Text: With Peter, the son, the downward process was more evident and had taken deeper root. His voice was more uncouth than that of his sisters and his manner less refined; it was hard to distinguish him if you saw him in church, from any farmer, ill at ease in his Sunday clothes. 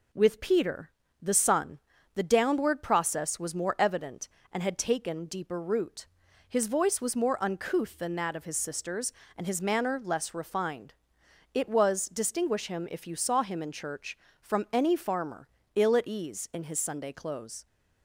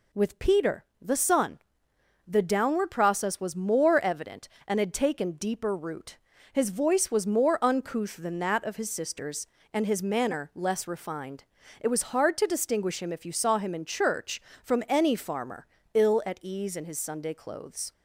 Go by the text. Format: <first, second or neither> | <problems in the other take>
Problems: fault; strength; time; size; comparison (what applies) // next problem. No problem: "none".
second | skips "hard to"; at 12.0 s